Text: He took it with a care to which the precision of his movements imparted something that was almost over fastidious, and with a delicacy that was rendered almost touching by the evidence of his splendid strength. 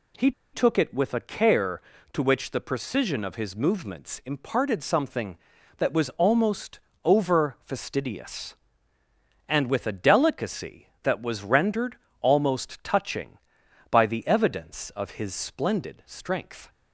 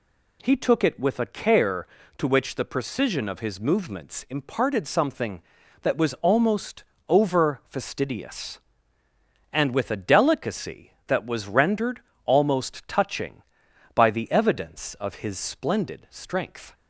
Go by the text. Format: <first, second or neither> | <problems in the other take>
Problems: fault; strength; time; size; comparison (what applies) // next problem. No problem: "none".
second | pauses between "He" and "took"; slight; at 0.3 s; 0.21 s long // pauses between "almost" and "over"; slight; at 6.7 s; 0.24 s long; slight in the second // pauses between "rendered" and "almost"; slight; at 11.9 s; 0.24 s long; slight in the second